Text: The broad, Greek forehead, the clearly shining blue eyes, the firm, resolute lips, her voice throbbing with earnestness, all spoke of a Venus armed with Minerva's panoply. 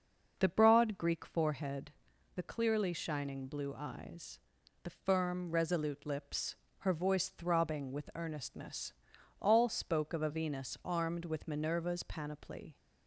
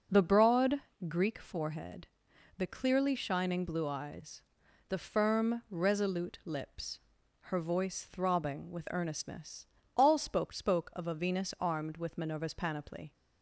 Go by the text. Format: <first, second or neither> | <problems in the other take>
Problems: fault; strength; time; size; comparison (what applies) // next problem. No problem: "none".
first | says "spoke" twice; at 10.5 s